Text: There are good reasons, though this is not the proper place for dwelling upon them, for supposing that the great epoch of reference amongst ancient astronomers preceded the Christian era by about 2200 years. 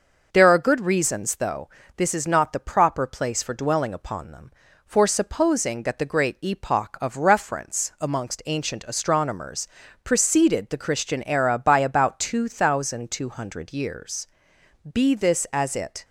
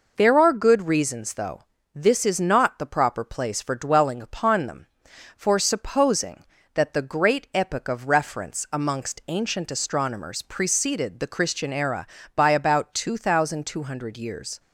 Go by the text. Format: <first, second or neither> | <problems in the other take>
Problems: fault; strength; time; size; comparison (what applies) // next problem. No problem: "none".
second | pauses between "though" and "this"; slight; at 1.6 s; 0.28 s long; slight in the second // pauses between "astronomers" and "preceded"; at 9.6 s; 0.38 s long // goes on to say "Be this as it"; noticeable; from 14.8 s on; 1.2 s long